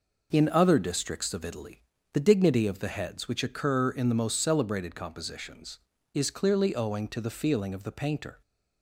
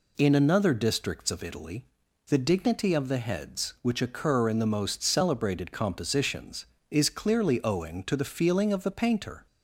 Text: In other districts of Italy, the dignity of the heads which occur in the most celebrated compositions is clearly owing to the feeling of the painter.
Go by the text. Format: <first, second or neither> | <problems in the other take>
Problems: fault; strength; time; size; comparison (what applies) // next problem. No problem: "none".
first | says "another" for "other"; at 0.3 s